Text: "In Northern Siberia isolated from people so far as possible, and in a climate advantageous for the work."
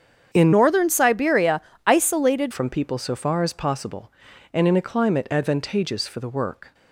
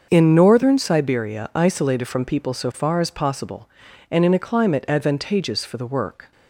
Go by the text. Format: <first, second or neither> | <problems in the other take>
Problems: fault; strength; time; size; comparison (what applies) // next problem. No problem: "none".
second | starts louder than the rest; strong; until 1.3 s; 7.5 dB; also in the second // changes voice from "Northern" to "isolated"; from 0.5 to 2.5 s; 2.0 s long // pauses between "Siberia" and "isolated"; slight; at 1.6 s; 0.26 s long